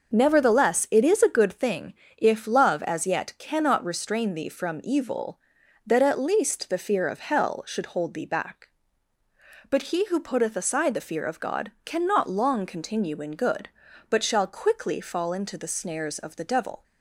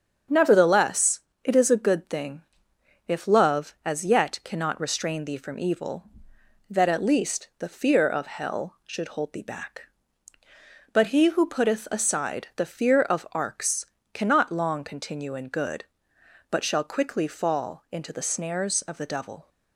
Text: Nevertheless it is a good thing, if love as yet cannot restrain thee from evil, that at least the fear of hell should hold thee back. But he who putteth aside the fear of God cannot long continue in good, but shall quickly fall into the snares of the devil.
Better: first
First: starts louder than the rest; noticeable; until 1.1 s; 6 dB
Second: starts louder than the rest; strong; until 1.5 s; 7.5 dB // pauses between "Nevertheless" and "it"; slight; at 1.2 s; 0.22 s long // says "Arks" for "God"; at 13.3 s

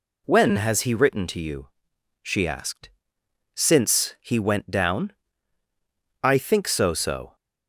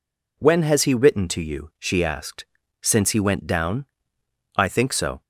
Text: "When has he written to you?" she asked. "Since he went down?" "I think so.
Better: second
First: says "so" twice; at 6.9 s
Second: none

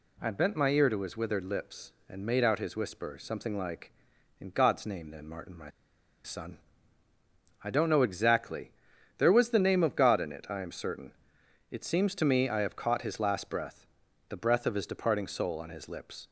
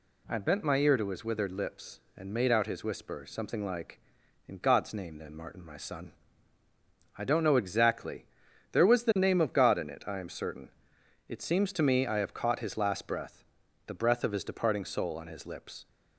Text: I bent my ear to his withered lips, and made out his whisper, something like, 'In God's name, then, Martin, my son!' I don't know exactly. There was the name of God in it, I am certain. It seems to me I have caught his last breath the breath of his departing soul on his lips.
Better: second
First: pauses between "my" and "son"; noticeable; at 5.6 s; 0.54 s long // pauses between "breath" and "the"; at 13.8 s; 0.44 s long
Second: pauses between "breath" and "the"; at 13.4 s; 0.44 s long

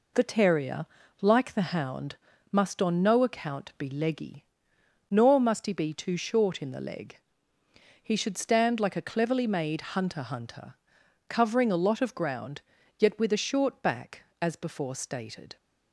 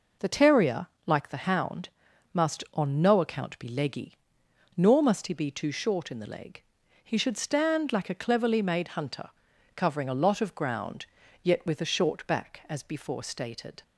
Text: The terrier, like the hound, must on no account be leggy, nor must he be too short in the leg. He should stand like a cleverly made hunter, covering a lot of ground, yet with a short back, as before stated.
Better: second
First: says "hunter" twice; at 10.2 s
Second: none

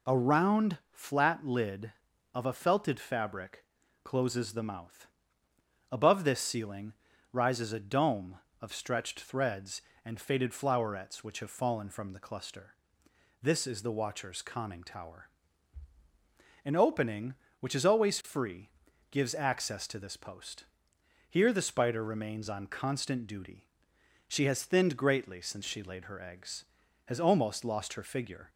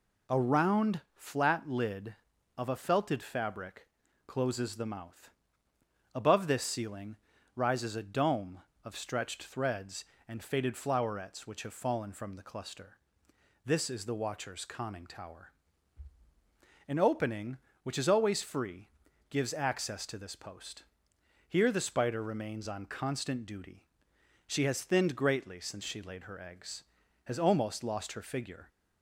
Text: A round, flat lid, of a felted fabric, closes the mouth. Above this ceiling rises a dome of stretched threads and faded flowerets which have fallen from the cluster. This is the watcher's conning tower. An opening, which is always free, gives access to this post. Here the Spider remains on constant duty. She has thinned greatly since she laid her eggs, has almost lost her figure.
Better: neither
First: pauses between "ceiling" and "rises"; at 6.9 s; 0.38 s long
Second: pauses between "ceiling" and "rises"; at 7.1 s; 0.38 s long

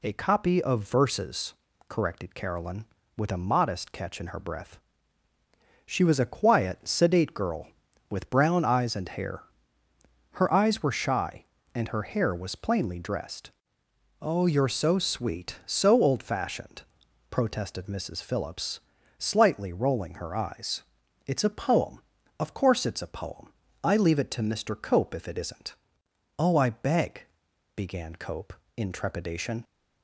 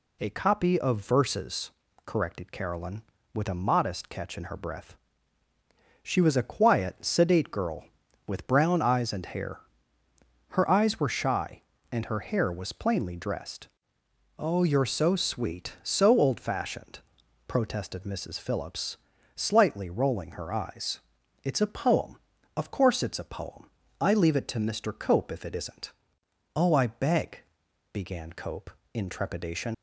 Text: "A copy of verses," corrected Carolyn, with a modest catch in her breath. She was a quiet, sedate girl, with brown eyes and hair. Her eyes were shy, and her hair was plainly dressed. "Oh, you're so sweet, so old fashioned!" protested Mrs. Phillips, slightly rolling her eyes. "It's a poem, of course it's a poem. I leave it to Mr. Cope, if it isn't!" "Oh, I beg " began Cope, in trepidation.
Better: first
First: none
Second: leaves "trepidation" unfinished; at 29.7 s; 60 ms

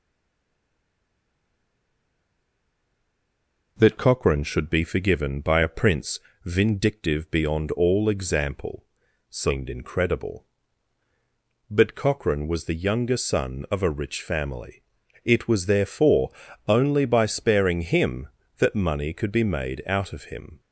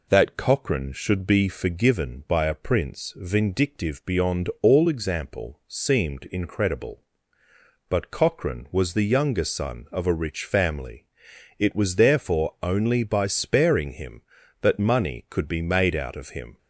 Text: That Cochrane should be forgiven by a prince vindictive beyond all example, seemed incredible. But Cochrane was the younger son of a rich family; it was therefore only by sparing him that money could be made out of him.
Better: second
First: stays silent before the first word; strong; until 3.7 s; 3.7 s long // pauses between "prince" and "vindictive"; slight; at 6.1 s; 0.28 s long // pauses between "therefore" and "only"; slight; at 16.3 s; 0.36 s long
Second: none

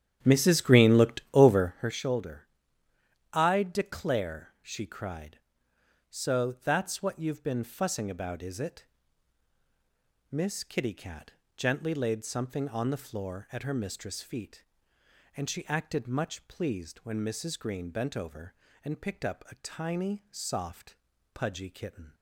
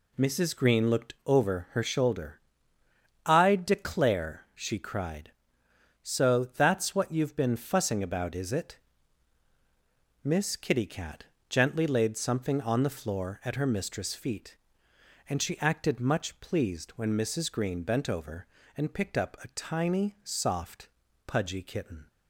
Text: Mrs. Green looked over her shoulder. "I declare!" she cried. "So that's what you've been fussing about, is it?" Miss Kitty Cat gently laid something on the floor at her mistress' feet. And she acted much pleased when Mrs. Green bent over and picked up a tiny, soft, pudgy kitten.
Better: second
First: starts louder than the rest; strong; until 1.9 s; 10 dB // pauses between "Cat" and "gently"; slight; at 11.3 s; 0.24 s long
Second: pauses between "Cat" and "gently"; slight; at 11.2 s; 0.24 s long

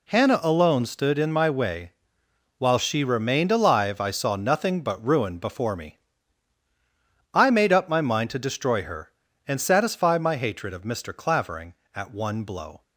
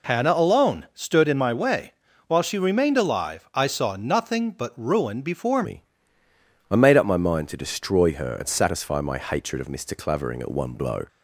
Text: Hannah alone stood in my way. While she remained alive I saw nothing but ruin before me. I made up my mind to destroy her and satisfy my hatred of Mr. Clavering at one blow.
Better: first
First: none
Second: changes voice at "me"; from 5.6 s on; 5.4 s long

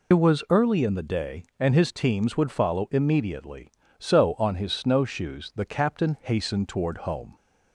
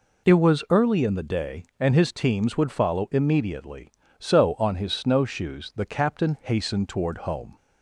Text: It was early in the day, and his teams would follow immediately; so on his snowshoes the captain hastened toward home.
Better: second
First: loses the start of "It"; at 0.1 s; 55 ms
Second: none

